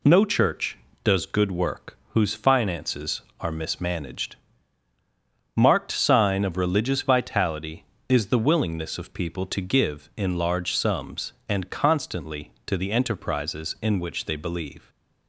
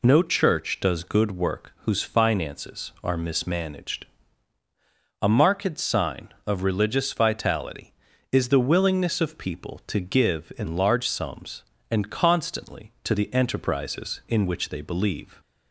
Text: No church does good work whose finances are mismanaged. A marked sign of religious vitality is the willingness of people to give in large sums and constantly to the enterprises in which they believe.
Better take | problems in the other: second | skips "A"; at 4.9 s

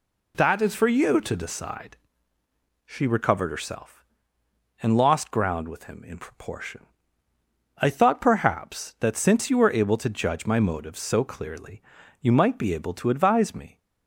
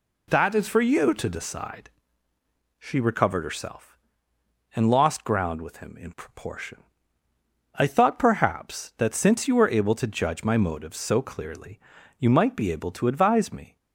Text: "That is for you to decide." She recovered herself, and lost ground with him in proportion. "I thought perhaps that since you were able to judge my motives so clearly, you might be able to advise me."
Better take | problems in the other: neither | none

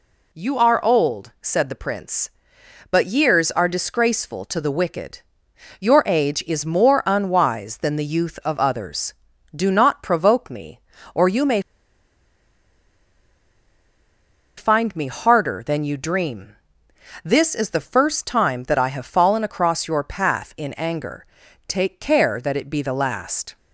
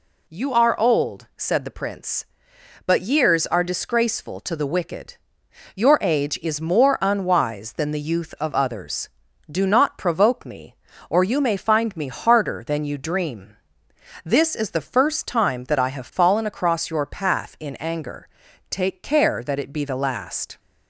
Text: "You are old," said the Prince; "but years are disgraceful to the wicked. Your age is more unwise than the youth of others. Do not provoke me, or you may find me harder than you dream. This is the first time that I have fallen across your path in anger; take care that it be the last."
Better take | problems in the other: second | pauses between "may" and "find"; strong; at 11.5 s; 2.9 s long

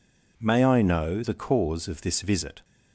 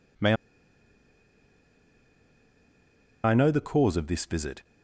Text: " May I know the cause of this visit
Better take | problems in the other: first | pauses between "May" and "I"; strong; at 0.3 s; 2.9 s long

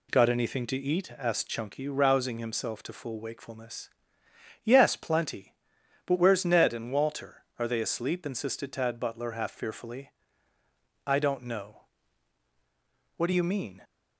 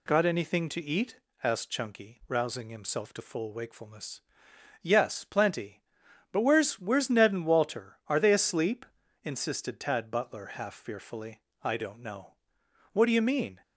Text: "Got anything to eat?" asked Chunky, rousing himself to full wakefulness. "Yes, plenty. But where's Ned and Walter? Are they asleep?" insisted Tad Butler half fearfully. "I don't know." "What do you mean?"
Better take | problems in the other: first | says "where's" twice; at 6.7 s

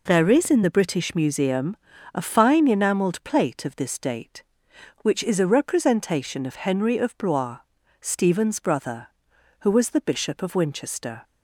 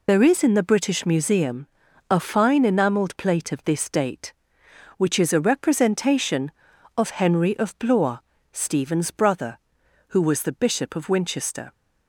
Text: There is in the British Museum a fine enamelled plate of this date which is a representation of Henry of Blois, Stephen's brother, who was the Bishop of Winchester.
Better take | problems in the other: first | loses the start of "There"; at 0.0 s; 30 ms // pauses between "Museum" and "a"; at 1.6 s; 0.44 s long; also in the first

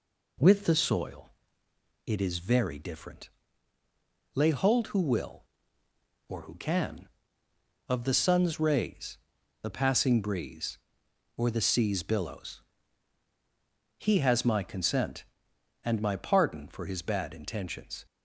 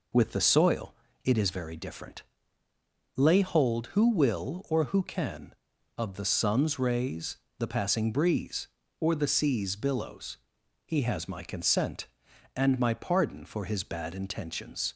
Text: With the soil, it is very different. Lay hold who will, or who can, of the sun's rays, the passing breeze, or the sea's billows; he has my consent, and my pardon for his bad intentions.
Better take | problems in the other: neither | none

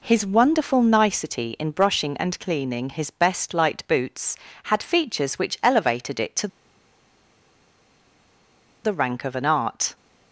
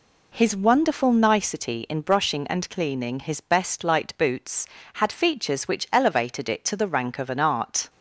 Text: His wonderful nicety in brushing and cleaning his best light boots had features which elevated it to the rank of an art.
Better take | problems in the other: second | pauses between "to" and "the"; strong; at 6.4 s; 2.3 s long

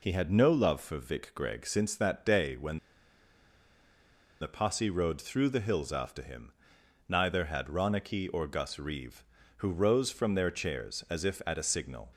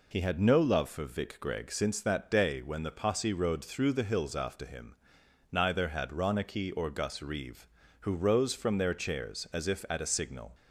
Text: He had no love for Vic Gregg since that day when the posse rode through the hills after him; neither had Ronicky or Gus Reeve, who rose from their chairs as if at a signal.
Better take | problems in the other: second | pauses between "when" and "the"; strong; at 2.7 s; 1.6 s long

